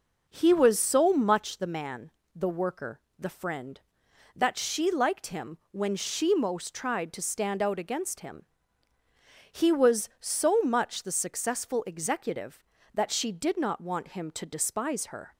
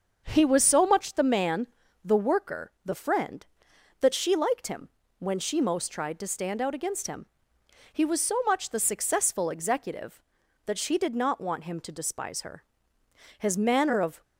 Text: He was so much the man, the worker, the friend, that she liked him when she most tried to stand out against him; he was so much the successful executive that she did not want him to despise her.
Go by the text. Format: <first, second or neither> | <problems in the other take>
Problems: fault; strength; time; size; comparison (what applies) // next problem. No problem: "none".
first | starts louder than the rest; until 1.2 s; 6.5 dB // pauses between "him" and "when"; slight; at 4.8 s; 0.30 s long // goes on to say "His manner of"; noticeable; from 13.3 s on; 0.84 s long